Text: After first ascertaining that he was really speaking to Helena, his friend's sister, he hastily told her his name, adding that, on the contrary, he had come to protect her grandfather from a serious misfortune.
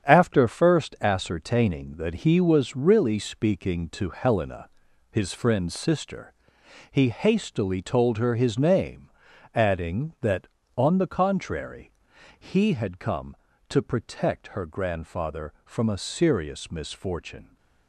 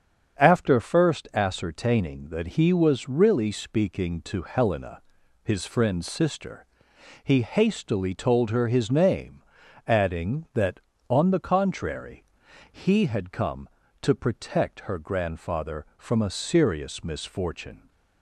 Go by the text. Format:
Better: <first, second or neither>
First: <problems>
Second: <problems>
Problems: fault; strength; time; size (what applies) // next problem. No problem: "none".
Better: second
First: gets quieter; strong; throughout; 8 dB // starts louder than the rest; strong; until 1.1 s; 8.5 dB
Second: starts louder than the rest; strong; until 1.4 s; 8 dB